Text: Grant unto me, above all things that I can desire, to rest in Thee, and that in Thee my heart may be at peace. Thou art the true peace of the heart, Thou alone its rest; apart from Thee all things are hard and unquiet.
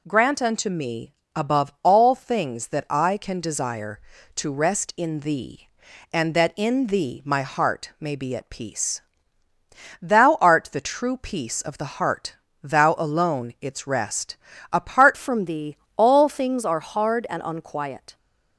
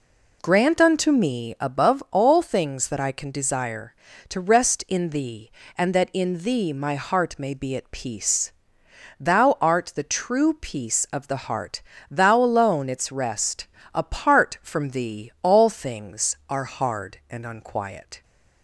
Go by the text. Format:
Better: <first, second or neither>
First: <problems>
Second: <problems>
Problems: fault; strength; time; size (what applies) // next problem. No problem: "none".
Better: second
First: changes voice at "from"; from 15.1 s on; 3.0 s long // pauses between "Thee" and "all"; slight; at 15.7 s; 0.18 s long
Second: none